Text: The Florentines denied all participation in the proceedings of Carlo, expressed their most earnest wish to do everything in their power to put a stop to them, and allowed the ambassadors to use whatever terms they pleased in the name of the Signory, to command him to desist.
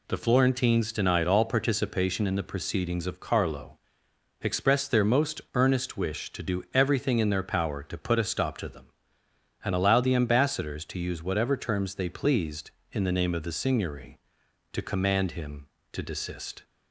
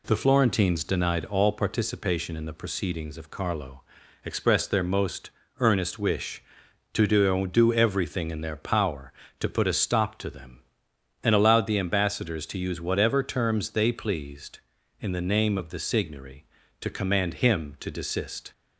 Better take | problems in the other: first | pauses between "most" and "earnest"; slight; at 5.3 s; 0.28 s long // says "do" twice; at 7.4 s

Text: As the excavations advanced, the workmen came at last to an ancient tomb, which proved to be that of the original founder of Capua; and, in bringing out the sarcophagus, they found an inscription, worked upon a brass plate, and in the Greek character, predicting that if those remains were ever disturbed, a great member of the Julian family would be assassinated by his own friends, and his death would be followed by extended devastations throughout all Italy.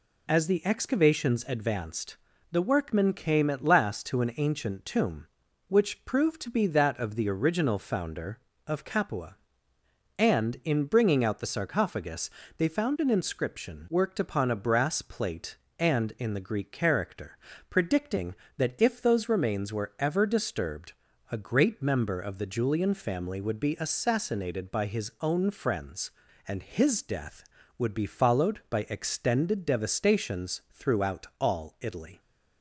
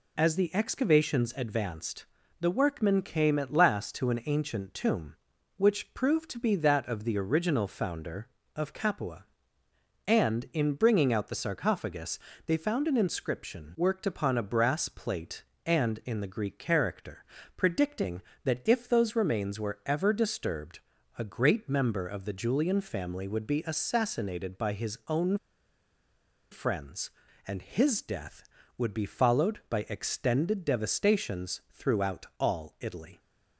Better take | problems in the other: first | pauses between "own" and "friends"; at 25.3 s; 1.1 s long

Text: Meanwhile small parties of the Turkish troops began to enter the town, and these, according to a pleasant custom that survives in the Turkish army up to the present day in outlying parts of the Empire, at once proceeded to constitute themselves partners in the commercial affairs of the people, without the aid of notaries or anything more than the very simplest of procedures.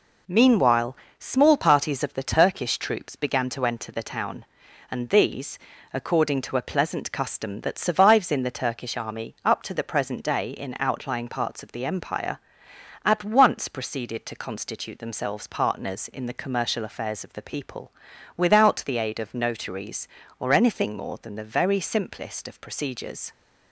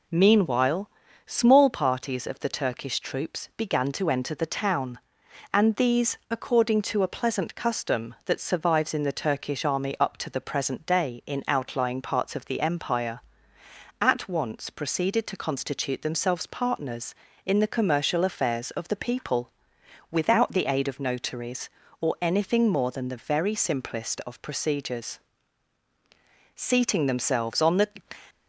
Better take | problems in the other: first | pauses between "Meanwhile" and "small"; slight; at 0.8 s; 0.36 s long; slight in the first // goes on to say "Seating themselves on the"; from 26.5 s on; 1.3 s long

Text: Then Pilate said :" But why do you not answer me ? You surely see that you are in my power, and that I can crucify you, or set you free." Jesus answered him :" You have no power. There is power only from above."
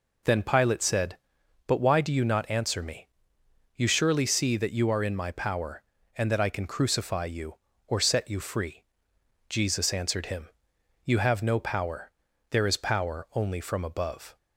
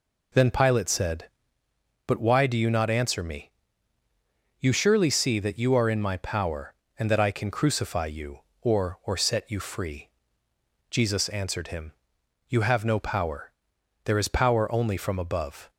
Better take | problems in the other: first | says "or" twice; at 9.0 s

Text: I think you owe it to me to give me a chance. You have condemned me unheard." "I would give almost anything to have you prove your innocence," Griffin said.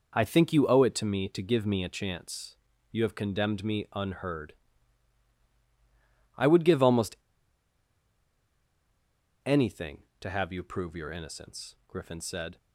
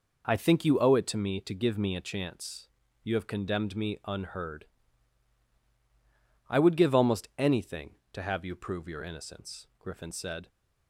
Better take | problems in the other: second | pauses between "almost" and "anything"; strong; at 7.1 s; 2.2 s long

